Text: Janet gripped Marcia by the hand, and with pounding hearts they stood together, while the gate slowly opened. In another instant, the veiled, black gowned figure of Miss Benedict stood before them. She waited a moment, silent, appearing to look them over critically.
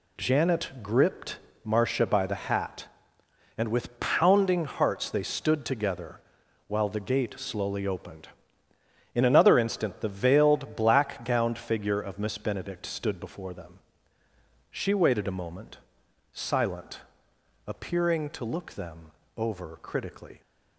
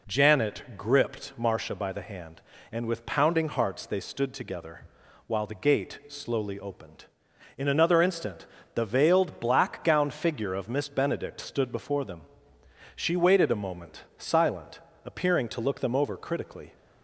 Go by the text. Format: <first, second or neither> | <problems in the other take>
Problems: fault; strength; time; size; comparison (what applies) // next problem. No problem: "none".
second | pauses between "gripped" and "Marcia"; slight; at 1.3 s; 0.26 s long // says "hat" for "hand"; at 2.3 s // pauses between "them" and "over"; slight; at 19.1 s; 0.26 s long